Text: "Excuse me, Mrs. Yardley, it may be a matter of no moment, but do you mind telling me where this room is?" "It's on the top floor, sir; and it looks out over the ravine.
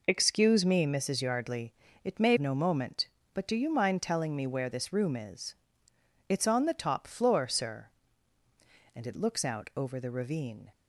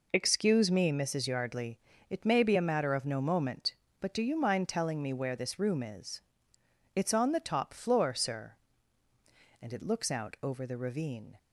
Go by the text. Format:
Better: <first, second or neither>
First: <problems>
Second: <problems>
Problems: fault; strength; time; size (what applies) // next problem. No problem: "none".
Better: second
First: skips "be a matter of"; at 2.3 s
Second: none